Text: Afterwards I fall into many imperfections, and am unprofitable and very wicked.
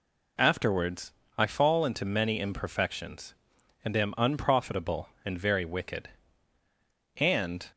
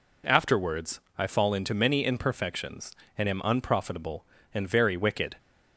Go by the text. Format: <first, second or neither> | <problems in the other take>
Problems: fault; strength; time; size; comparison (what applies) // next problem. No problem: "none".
second | pauses between "Afterwards" and "I"; slight; at 1.1 s; 0.24 s long; slight in the second // goes on to say "And"; slight; from 7.1 s on; 0.46 s long